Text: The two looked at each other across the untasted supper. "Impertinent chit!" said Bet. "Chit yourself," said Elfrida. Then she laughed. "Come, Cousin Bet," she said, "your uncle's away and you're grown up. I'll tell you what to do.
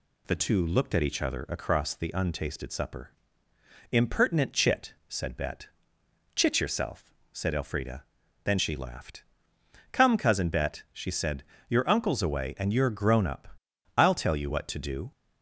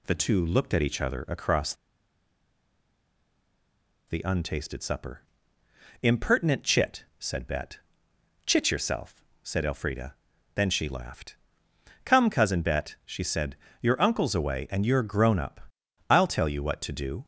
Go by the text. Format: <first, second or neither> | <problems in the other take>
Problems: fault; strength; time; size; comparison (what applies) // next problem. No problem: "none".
first | pauses between "across" and "the"; strong; at 1.7 s; 2.3 s long